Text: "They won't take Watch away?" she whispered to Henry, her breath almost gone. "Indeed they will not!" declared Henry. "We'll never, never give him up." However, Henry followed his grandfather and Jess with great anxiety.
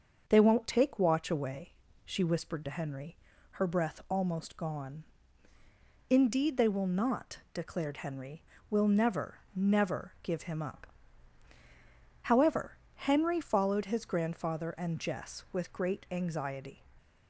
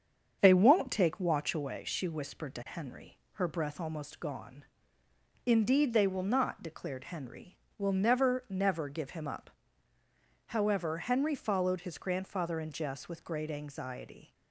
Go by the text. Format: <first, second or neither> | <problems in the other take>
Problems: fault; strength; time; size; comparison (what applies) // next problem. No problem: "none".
neither | starts louder than the rest; the same in both